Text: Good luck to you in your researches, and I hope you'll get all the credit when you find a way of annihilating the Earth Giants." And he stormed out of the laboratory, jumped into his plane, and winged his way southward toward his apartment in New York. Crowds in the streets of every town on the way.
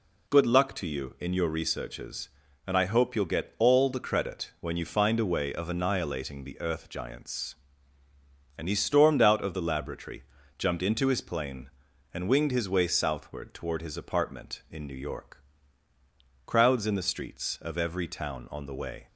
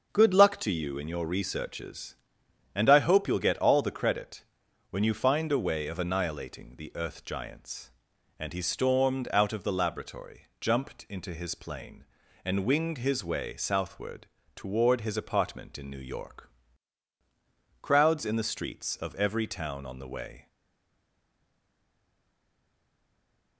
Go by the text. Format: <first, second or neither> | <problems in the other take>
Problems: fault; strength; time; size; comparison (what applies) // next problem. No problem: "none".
first | starts louder than the rest; until 1.1 s; 6.5 dB // pauses between "credit" and "when"; noticeable; at 4.4 s; 0.46 s long // pauses between "southward" and "toward"; slight; at 14.2 s; 0.30 s long // stays silent after the last word; strong; from 20.4 s on; 3.1 s long